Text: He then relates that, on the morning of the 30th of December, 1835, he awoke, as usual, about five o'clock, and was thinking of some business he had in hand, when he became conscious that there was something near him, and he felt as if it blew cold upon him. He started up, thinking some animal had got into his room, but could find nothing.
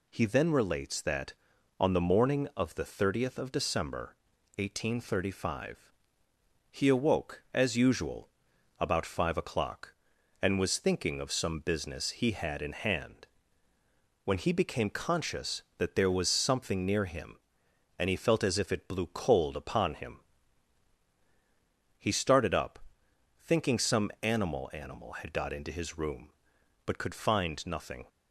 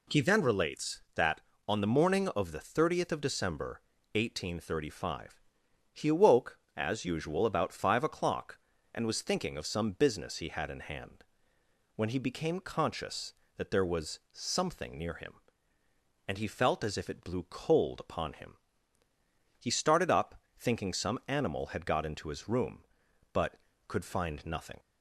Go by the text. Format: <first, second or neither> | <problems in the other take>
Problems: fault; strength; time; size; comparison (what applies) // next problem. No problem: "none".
second | says "animal" twice; at 24.7 s